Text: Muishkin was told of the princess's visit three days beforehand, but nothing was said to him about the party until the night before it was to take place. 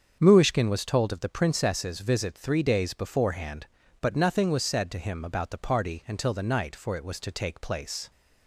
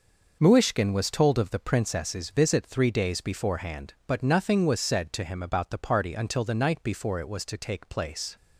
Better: second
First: starts louder than the rest; until 1.2 s; 7 dB // says "for" for "before"; at 6.7 s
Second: none

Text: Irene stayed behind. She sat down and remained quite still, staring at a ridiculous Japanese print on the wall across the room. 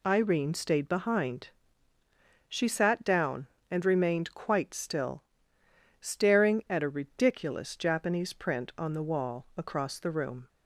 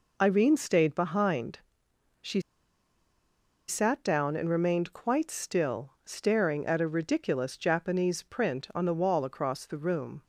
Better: first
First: none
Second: pauses between "She" and "sat"; strong; at 2.4 s; 1.2 s long

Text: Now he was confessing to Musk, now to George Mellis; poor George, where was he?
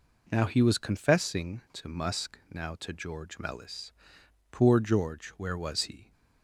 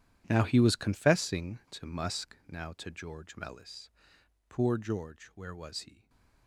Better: first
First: none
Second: gets quieter; strong; throughout; 16 dB // stays silent after the last word; slight; from 5.9 s on; 0.5 s long

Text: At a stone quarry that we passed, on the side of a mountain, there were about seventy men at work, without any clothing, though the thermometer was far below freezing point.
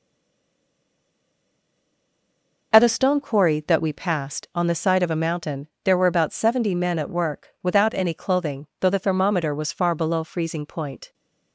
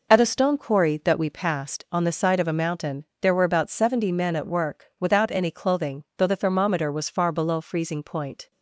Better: second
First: stays silent before the first word; strong; until 2.7 s; 2.7 s long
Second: none

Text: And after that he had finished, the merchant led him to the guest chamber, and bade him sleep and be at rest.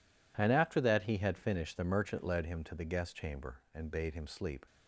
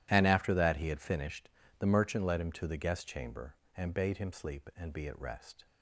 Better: second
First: stops before "and be at rest"; at 4.6 s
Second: none

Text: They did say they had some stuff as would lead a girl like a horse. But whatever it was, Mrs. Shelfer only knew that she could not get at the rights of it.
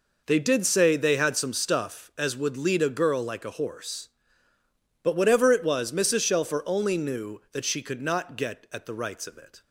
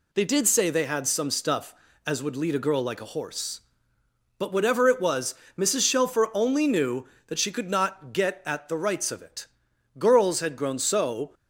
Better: first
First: none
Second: goes on to say "Girls had grown so"; from 9.9 s on; 1.3 s long

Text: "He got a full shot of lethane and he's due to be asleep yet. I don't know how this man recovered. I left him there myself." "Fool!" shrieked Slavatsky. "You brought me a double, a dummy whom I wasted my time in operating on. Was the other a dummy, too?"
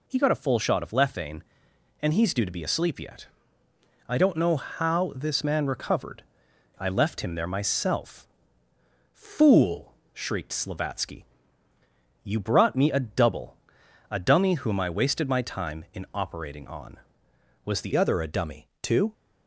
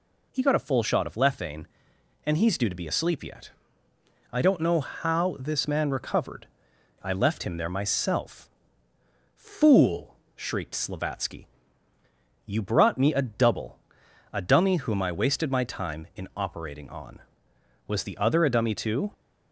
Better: second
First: changes voice at "other"; from 17.9 s on; 1.2 s long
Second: none

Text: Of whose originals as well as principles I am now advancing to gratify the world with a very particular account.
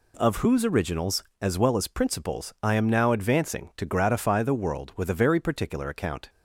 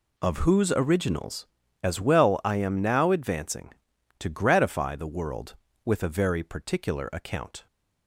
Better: first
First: none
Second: skips "as principles"; at 2.4 s

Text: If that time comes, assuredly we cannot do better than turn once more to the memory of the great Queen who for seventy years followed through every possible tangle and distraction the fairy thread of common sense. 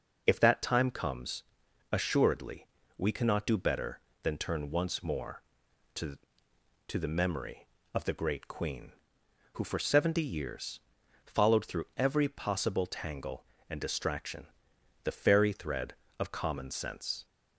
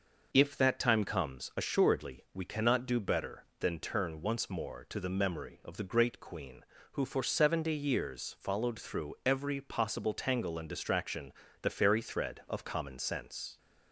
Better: second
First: pauses between "assuredly" and "we"; slight; at 2.6 s; 0.30 s long // says "to" twice; at 6.8 s // pauses between "years" and "followed"; at 10.8 s; 0.44 s long // pauses between "distraction" and "the"; noticeable; at 14.4 s; 0.56 s long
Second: pauses between "distraction" and "the"; slight; at 11.3 s; 0.30 s long

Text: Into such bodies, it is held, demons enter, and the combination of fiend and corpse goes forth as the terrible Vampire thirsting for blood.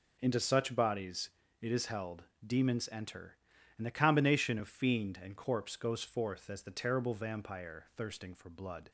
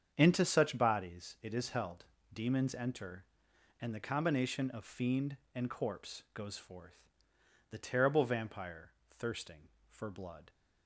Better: first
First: none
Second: starts louder than the rest; strong; until 1.1 s; 7.5 dB // skips "as"; at 7.3 s // pauses between "Vampire" and "thirsting"; slight; at 8.9 s; 0.20 s long

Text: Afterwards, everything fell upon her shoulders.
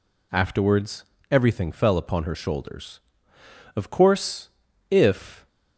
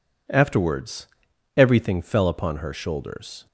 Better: second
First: goes on to say "Of course if"; strong; from 3.7 s on; 1.7 s long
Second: none

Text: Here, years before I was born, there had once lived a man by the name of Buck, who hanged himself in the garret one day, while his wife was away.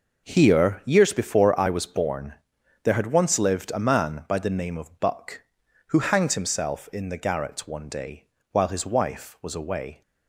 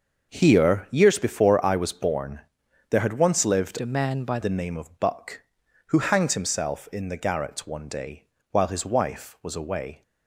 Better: first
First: none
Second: starts louder than the rest; noticeable; until 1.3 s; 6 dB // changes voice from "a" to "by"; from 3.8 to 4.3 s; 0.5 s long

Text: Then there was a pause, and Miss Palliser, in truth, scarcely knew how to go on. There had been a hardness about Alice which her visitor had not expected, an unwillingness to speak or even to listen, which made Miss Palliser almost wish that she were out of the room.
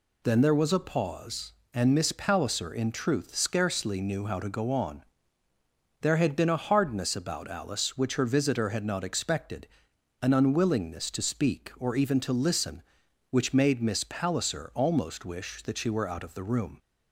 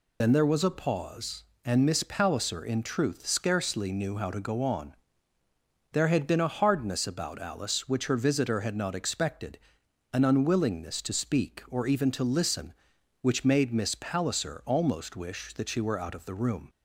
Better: first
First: none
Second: loses the start of "Then"; at 0.2 s; 50 ms

